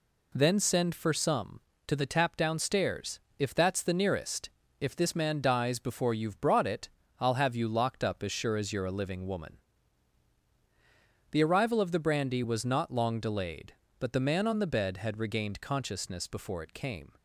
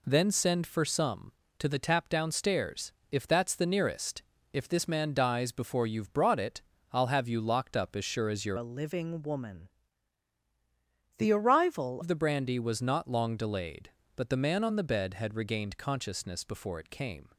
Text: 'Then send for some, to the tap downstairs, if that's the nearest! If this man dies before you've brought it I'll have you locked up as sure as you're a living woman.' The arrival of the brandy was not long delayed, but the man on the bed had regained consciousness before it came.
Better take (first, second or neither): first